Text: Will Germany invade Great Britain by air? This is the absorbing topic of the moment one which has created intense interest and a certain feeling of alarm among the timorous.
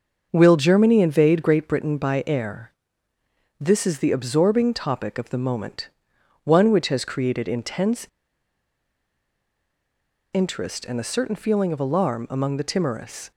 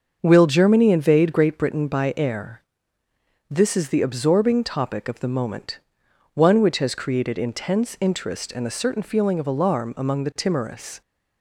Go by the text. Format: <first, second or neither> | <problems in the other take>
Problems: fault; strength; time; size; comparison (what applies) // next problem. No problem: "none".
second | starts louder than the rest; until 1.3 s; 6.5 dB; also in the second // pauses between "moment" and "one"; noticeable; at 5.8 s; 0.54 s long; noticeable in the second // pauses between "intense" and "interest"; strong; at 8.0 s; 2.2 s long